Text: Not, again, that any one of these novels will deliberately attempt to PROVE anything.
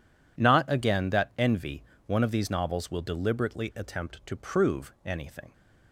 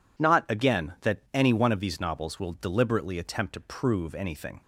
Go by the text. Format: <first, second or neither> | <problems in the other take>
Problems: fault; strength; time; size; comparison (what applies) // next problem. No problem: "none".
second | says "envy" for "any"; at 1.3 s